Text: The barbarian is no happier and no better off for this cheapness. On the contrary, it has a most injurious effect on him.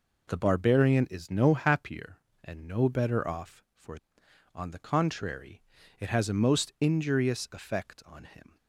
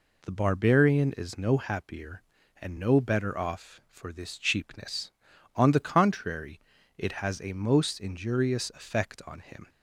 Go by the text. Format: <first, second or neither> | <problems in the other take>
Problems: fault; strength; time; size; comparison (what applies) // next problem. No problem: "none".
second | skips "this cheapness"; at 4.2 s